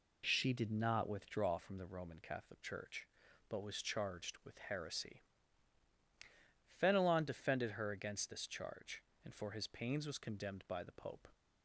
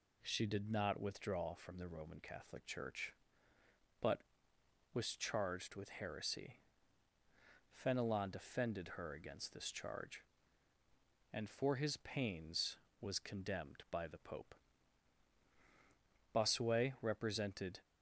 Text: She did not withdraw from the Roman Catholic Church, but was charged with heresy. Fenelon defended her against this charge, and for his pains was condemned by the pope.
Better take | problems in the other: first | goes on to say "Bossuet represented"; from 16.3 s on; 1.4 s long

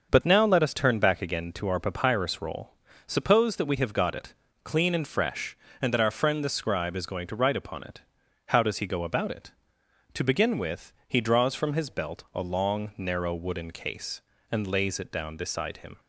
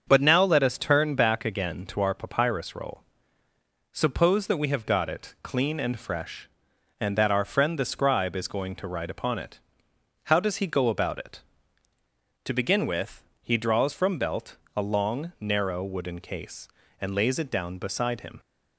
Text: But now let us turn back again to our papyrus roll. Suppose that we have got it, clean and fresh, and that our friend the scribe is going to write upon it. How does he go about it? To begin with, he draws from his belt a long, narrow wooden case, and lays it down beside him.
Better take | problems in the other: first | starts louder than the rest; until 1.1 s; 7 dB; also in the first // skips "his"; at 14.1 s // pauses between "belt" and "a"; slight; at 14.5 s; 0.20 s long

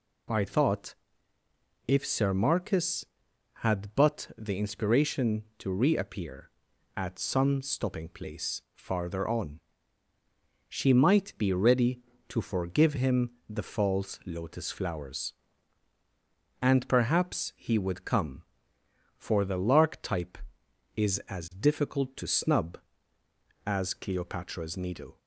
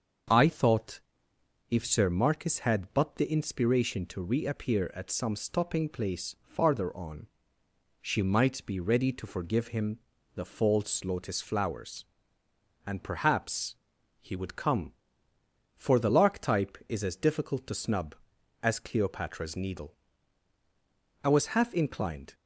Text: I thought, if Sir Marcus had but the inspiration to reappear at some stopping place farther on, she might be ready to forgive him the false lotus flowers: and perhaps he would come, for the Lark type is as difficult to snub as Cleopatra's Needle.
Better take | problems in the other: first | starts louder than the rest; until 2.0 s; 6.5 dB // pauses between "him" and "the"; at 9.9 s; 0.38 s long; slight in the first // pauses between "perhaps" and "he"; noticeable; at 13.7 s; 0.46 s long // goes on to say "I was half inclined"; noticeable; from 21.2 s on; 1.1 s long

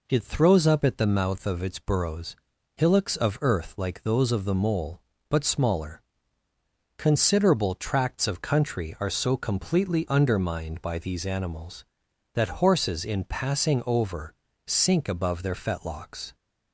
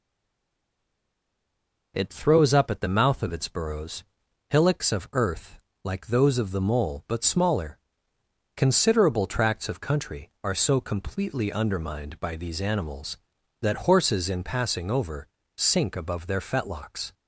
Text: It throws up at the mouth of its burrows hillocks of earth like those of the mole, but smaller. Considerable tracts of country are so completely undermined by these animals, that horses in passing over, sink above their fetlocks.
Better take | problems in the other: first | stays silent before the first word; noticeable; until 1.9 s; 1.9 s long // pauses between "burrows" and "hillocks"; noticeable; at 4.0 s; 0.46 s long; also in the first // pauses between "earth" and "like"; slight; at 5.5 s; 0.24 s long

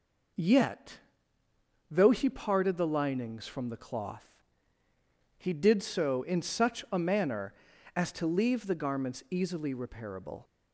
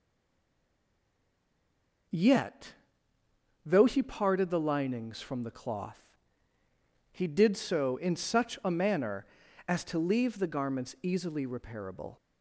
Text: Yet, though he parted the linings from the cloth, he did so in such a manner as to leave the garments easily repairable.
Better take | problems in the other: first | stays silent before the first word; until 2.0 s; 2.0 s long

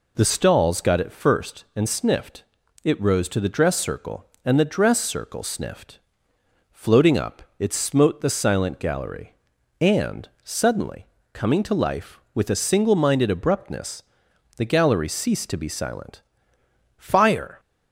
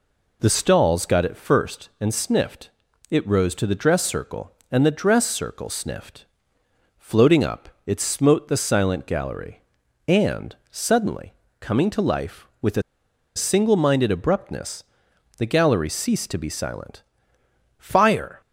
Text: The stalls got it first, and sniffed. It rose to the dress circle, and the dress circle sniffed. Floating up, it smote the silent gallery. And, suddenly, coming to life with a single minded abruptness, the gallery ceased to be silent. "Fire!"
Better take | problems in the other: first | pauses between "a" and "single"; noticeable; at 12.8 s; 0.54 s long

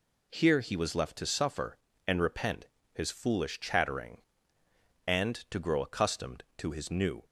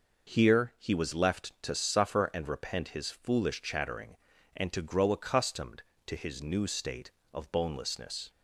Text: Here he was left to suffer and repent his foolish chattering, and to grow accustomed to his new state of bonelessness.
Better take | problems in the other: second | pauses between "repent" and "his"; slight; at 2.6 s; 0.26 s long // stops before "state of bonelessness"; at 7.2 s

